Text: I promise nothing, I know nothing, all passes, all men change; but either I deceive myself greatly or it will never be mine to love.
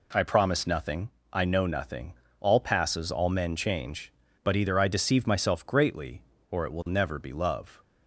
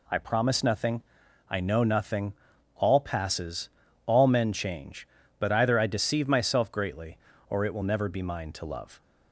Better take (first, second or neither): second